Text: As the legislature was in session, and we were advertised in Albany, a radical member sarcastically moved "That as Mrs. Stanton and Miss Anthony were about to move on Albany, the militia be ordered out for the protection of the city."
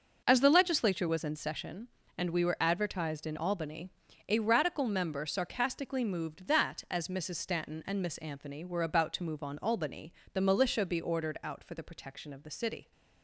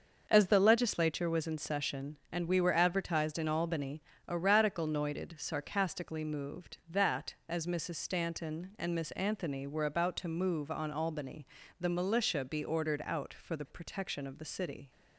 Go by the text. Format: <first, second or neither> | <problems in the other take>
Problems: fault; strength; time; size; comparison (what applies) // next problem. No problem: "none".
first | starts louder than the rest; until 1.2 s; 6 dB // says "noited" for "member"; at 4.8 s